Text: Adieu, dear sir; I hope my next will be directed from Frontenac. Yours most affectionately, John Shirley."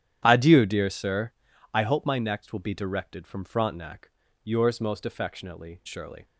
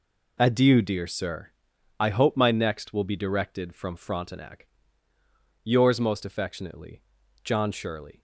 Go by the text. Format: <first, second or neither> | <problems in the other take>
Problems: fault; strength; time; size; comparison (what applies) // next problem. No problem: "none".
second | starts louder than the rest; strong; until 1.2 s; 10.5 dB // skips "John"; at 5.8 s